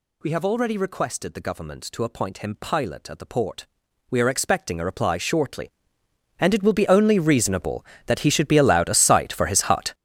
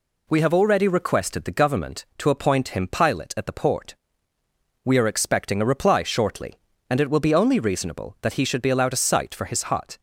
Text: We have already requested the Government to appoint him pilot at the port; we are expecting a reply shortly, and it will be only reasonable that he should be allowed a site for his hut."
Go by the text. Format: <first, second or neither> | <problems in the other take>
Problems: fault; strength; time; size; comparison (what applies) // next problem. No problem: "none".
second | gets louder; strong; throughout; 13 dB